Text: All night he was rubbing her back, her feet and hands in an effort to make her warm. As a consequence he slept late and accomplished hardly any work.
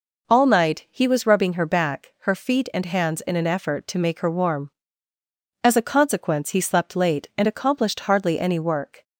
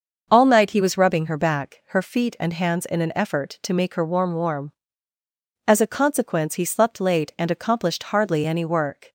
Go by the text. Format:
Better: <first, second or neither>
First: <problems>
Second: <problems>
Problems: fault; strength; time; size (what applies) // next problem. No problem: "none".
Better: first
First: none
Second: starts louder than the rest; until 1.3 s; 6.5 dB // says "warm" twice; at 4.3 s